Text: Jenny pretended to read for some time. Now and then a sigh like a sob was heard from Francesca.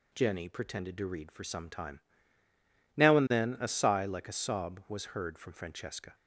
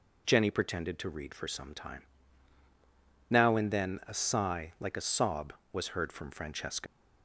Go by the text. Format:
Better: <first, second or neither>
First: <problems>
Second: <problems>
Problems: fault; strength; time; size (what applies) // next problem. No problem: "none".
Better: first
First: none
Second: leaves "Francesca" unfinished; at 6.8 s; 90 ms